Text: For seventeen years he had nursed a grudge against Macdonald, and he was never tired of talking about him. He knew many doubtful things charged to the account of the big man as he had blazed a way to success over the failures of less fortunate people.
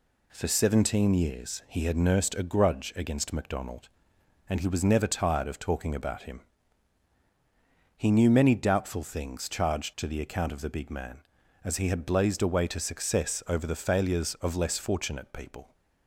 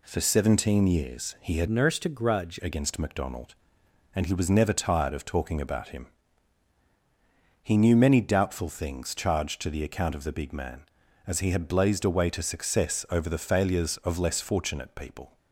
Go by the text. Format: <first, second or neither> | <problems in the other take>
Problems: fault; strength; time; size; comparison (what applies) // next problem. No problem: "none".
first | changes voice from "nursed" to "grudge"; from 1.6 to 2.5 s; 0.9 s long